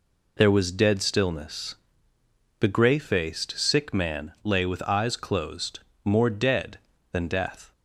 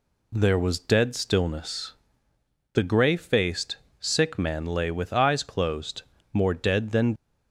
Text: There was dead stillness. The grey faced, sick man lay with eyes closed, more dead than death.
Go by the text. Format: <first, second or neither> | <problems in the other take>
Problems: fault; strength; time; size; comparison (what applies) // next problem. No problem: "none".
first | stops before "death"; at 7.1 s